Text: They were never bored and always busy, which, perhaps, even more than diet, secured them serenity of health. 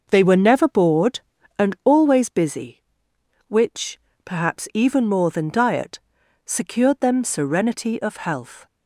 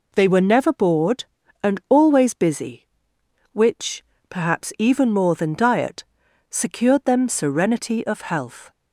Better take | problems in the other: second | starts louder than the rest; noticeable; until 1.9 s; 6 dB

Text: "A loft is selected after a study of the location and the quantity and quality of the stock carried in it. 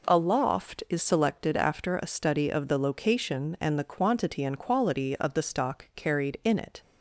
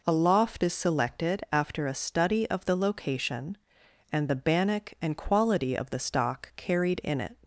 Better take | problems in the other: first | says "bannock" for "quantity"; at 4.3 s

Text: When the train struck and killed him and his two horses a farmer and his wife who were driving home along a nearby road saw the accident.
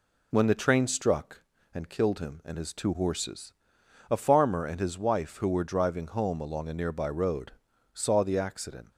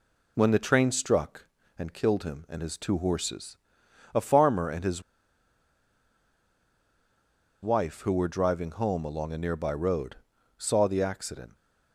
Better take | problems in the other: first | pauses between "horses" and "a"; noticeable; at 3.5 s; 0.56 s long; noticeable in the first // pauses between "his" and "wife"; strong; at 5.0 s; 2.6 s long // pauses between "road" and "saw"; at 10.1 s; 0.42 s long; also in the first

